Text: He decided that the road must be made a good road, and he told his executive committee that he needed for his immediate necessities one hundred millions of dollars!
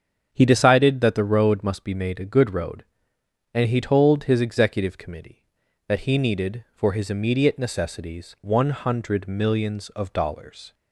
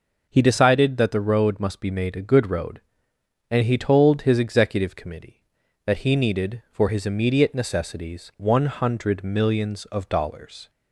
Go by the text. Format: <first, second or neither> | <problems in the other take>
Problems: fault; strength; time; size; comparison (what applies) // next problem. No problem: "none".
second | starts louder than the rest; strong; until 1.9 s; 7.5 dB